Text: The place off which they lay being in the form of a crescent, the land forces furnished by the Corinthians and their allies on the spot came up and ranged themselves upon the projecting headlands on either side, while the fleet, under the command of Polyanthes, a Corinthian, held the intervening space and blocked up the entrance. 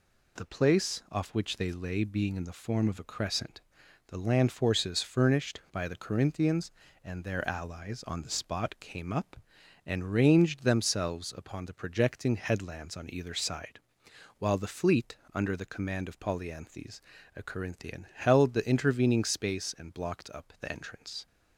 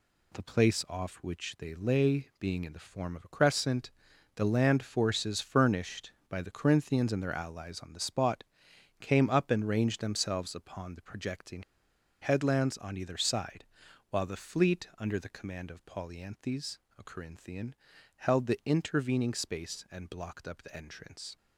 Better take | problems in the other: first | pauses between "spot" and "came"; noticeable; at 8.4 s; 0.56 s long // pauses between "projecting" and "headlands"; noticeable; at 11.6 s; 0.60 s long

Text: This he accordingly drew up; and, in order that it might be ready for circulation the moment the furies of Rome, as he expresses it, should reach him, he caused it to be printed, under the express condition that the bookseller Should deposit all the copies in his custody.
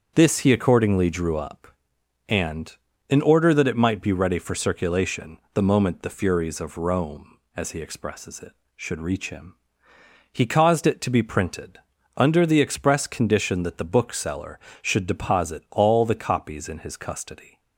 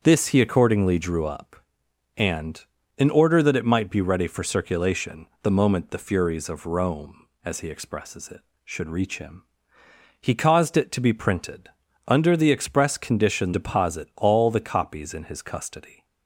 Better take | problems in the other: first | starts louder than the rest; strong; until 1.0 s; 7 dB; strong in the first // pauses between "circulation" and "the"; slight; at 5.2 s; 0.16 s long; slight in the first // skips "that the bookseller Should"; at 13.5 s

